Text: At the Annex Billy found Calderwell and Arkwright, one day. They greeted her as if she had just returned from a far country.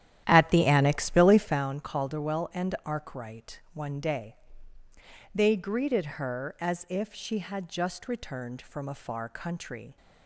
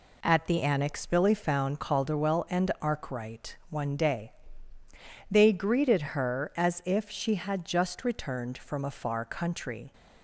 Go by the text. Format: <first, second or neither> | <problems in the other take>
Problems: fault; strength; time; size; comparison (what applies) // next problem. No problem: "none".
second | starts louder than the rest; strong; until 1.7 s; 11.5 dB